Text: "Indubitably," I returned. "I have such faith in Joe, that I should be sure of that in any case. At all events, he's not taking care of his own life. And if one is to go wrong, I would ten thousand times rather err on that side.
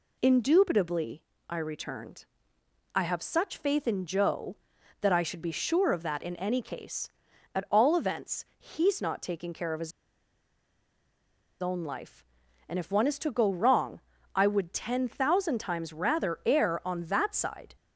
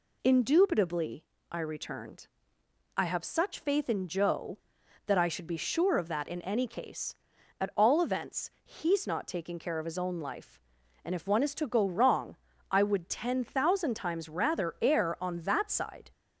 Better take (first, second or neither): second